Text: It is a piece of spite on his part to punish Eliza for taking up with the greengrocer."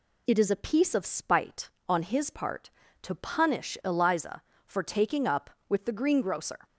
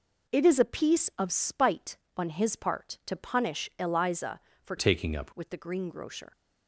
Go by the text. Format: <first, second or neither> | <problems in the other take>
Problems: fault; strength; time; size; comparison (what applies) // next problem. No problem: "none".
first | changes voice from "taking" to "up"; from 4.7 to 5.3 s; 0.6 s long